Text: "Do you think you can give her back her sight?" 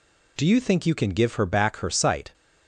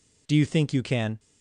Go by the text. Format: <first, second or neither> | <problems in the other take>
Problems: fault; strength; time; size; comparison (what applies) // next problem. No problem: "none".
first | stops before "give her back her sight"; at 1.1 s